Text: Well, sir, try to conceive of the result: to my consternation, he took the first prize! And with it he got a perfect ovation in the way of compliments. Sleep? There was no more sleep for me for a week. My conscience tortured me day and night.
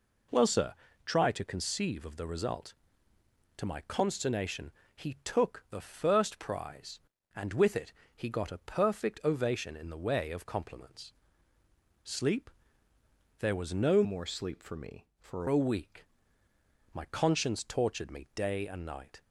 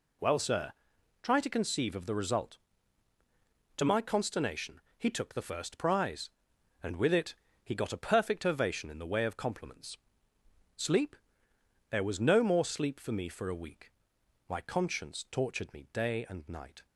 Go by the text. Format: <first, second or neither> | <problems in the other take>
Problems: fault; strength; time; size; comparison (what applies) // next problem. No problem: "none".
second | pauses between "it" and "he"; slight; at 7.9 s; 0.20 s long; slight in the second // changes voice from "more" to "for"; from 14.0 to 15.4 s; 1.4 s long